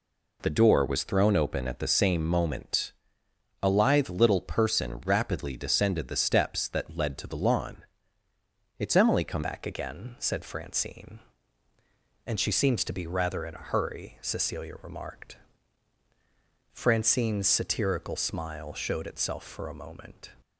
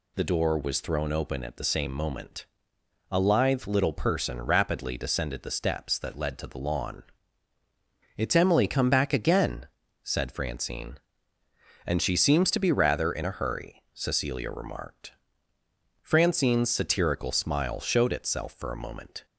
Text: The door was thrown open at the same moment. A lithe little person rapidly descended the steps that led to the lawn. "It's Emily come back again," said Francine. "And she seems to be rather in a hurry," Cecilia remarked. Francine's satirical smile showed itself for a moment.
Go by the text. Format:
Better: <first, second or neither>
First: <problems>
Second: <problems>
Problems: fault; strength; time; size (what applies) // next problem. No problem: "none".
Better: second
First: changes voice at "back"; from 9.4 s on; 10.9 s long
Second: none